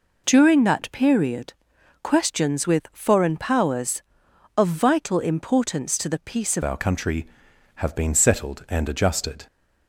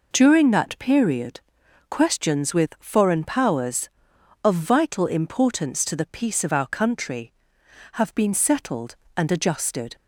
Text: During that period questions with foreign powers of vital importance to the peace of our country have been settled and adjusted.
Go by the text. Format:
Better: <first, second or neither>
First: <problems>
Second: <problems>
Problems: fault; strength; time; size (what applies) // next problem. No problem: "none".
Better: second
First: pauses between "period" and "questions"; noticeable; at 1.5 s; 0.48 s long // changes voice at "our"; from 6.6 s on; 2.8 s long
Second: pauses between "period" and "questions"; noticeable; at 1.3 s; 0.48 s long